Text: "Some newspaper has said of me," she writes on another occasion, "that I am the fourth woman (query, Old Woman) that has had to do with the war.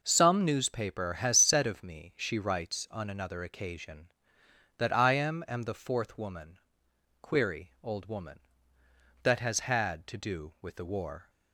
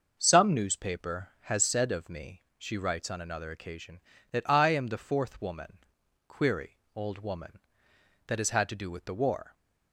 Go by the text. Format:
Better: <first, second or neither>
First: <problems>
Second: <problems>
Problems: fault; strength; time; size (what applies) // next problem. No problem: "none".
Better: second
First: says "am" twice; at 5.4 s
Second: none